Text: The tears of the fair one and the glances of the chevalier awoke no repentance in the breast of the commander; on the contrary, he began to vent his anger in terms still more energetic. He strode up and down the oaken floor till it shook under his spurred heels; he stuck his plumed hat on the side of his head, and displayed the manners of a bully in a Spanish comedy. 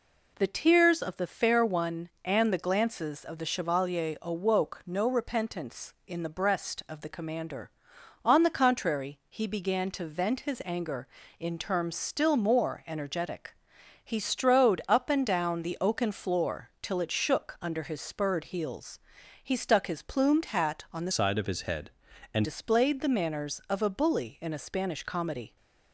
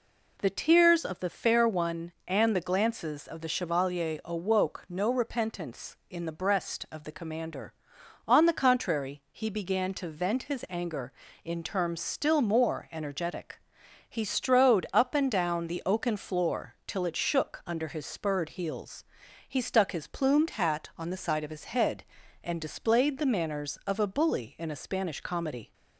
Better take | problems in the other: second | changes voice from "side" to "and"; from 21.1 to 22.4 s; 1.3 s long

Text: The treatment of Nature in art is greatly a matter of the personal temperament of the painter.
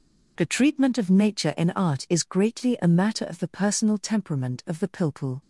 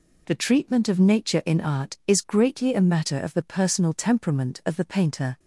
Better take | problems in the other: second | says "pilpul" for "painter"; at 4.8 s

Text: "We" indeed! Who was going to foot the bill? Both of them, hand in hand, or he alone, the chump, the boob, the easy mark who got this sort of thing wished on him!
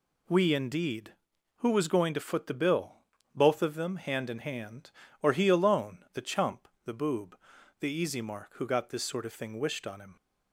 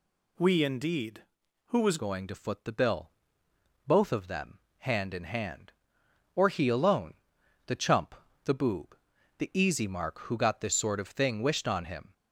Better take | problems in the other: first | changes voice at "going"; from 1.9 s on; 10.2 s long

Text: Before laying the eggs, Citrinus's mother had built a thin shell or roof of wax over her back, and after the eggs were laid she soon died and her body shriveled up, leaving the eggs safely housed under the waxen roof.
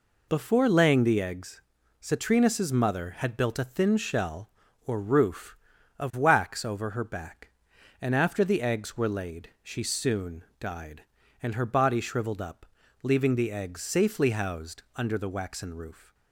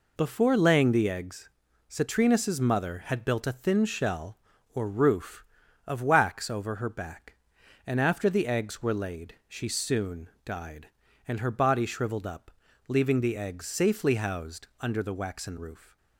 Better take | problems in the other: neither | none

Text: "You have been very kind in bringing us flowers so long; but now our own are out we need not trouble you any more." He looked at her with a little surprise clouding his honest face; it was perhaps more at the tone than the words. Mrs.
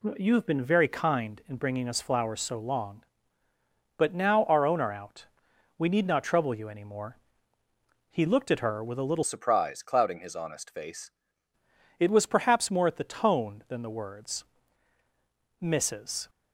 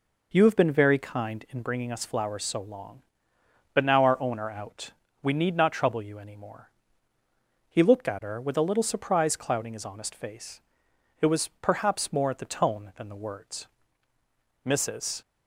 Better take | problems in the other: second | pauses between "out" and "we"; noticeable; at 5.2 s; 0.50 s long; slight in the second // changes voice from "surprise" to "face"; from 9.2 to 11.1 s; 1.9 s long

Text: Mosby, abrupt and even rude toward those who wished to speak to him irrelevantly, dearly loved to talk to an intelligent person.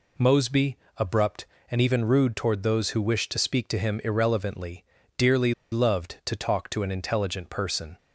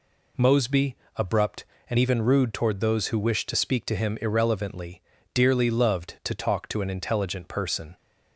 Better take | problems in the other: second | pauses between "dearly" and "loved"; slight; at 5.5 s; 0.19 s long

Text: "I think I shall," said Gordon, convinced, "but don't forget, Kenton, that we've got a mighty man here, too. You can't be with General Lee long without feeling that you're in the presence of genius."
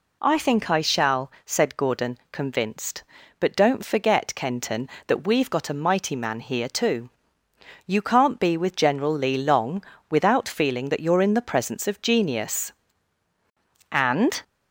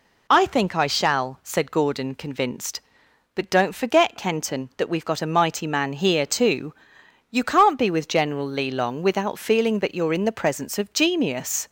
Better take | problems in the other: second | pauses between "long" and "without"; slight; at 9.8 s; 0.26 s long // goes on to say "And"; from 13.9 s on; 0.50 s long

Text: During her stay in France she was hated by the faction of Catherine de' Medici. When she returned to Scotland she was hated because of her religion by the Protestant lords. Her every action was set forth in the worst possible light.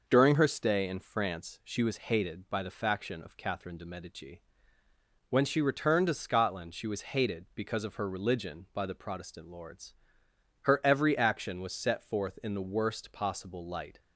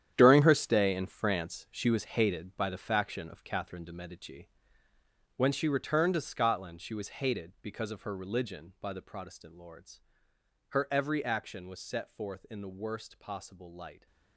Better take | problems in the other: first | gets quieter; strong; throughout; 12 dB

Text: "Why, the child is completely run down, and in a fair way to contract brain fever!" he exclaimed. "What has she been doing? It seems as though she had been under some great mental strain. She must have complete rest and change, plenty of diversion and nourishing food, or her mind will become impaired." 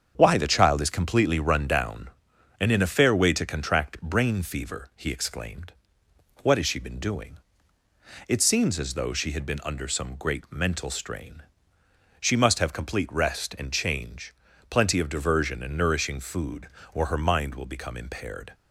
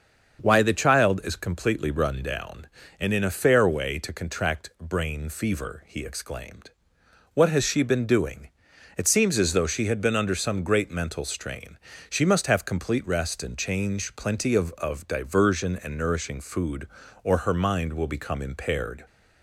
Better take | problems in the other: first | starts louder than the rest; until 1.4 s; 7 dB; strong in the first // says "of" twice; at 14.7 s

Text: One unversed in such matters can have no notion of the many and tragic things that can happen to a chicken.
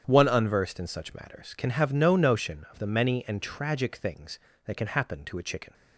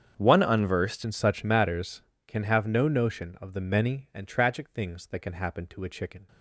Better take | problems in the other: first | starts louder than the rest; strong; until 1.1 s; 7.5 dB; strong in the first // changes voice at "in"; from 1.0 s on; 5.2 s long

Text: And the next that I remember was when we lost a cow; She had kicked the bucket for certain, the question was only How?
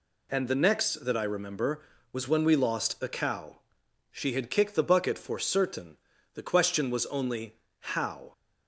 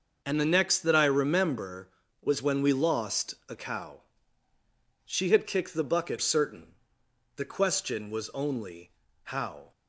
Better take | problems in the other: first | starts louder than the rest; until 1.2 s; 6 dB // skips "for"; at 6.1 s // pauses between "only" and "How"; slight; at 8.9 s; 0.32 s long; slight in the first

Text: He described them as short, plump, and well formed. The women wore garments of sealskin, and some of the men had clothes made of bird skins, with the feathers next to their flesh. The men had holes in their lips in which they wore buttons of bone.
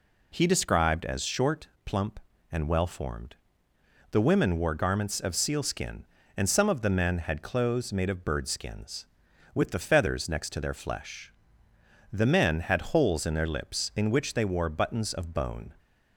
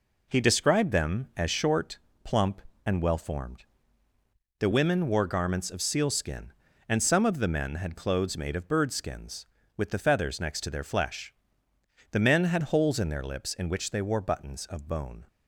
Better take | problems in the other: second | skips "them"; at 1.0 s

